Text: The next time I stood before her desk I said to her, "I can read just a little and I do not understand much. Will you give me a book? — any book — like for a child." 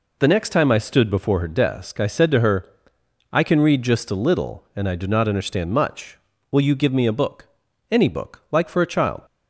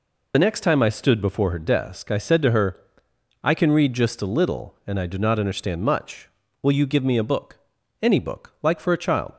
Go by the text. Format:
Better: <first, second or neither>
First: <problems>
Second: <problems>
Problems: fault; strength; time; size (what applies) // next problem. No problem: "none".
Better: first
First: none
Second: loses the start of "The"; at 0.3 s; 35 ms